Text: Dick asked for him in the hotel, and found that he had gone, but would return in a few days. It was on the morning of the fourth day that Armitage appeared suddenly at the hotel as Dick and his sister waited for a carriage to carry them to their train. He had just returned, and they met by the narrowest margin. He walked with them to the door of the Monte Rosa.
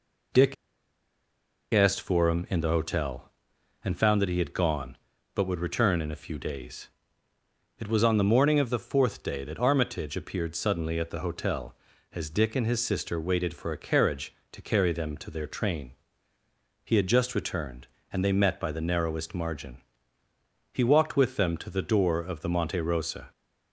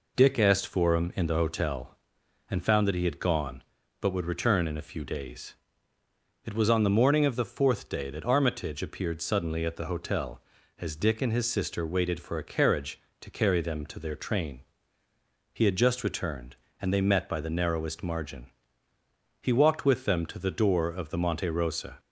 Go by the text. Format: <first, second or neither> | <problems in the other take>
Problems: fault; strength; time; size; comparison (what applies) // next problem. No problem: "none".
second | pauses between "Dick" and "asked"; at 0.5 s; 1.1 s long